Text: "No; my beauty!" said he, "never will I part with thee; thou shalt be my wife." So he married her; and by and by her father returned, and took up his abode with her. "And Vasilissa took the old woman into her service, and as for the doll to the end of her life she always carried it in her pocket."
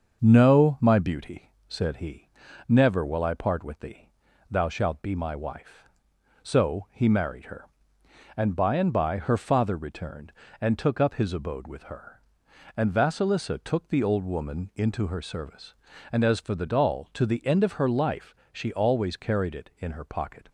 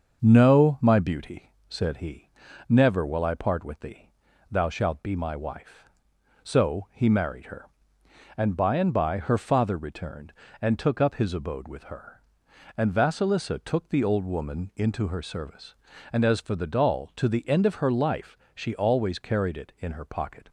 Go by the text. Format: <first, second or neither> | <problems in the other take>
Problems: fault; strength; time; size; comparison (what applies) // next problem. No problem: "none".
neither | starts louder than the rest; the same in both // pauses between "life" and "she"; slight; the same in both